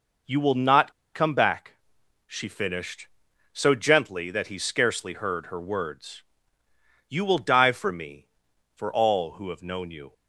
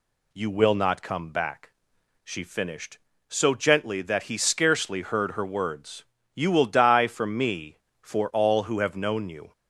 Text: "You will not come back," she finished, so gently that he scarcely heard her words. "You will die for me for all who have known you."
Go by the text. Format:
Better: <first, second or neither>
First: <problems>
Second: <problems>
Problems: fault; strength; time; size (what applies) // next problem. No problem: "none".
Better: second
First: pauses between "not" and "come"; slight; at 0.9 s; 0.22 s long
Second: none